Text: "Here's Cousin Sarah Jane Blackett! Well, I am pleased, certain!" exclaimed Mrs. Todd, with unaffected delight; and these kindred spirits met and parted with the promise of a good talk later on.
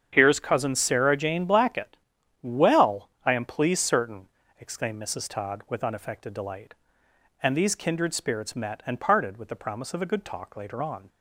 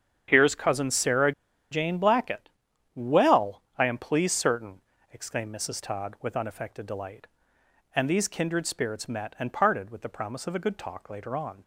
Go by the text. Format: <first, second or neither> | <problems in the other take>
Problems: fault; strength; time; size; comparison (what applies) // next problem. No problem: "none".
first | starts louder than the rest; strong; until 1.2 s; 8 dB; strong in the first // pauses between "Sarah" and "Jane"; at 1.3 s; 0.40 s long